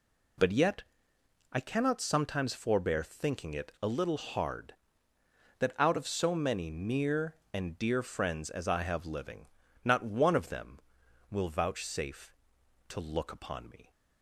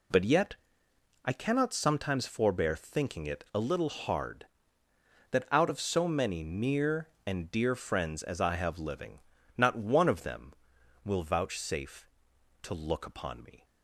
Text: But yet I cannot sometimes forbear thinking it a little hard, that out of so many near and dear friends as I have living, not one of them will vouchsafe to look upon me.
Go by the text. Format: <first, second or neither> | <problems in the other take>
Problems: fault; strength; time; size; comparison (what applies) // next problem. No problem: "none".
neither | pauses between "yet" and "I"; noticeable; the same in both